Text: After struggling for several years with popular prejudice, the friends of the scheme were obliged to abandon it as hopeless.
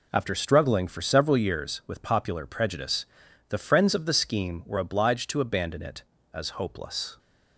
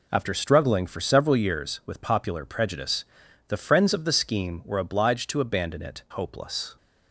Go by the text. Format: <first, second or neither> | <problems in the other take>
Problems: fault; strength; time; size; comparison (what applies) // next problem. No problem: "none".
first | skips "as"; at 6.0 s